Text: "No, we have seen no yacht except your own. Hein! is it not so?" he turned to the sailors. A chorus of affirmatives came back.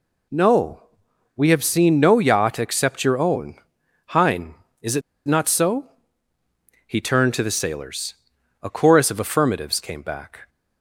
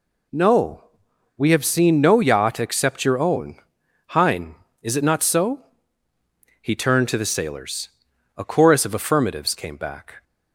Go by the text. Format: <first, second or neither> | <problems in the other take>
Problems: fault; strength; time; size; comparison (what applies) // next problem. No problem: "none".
second | pauses between "it" and "not"; slight; at 5.0 s; 0.27 s long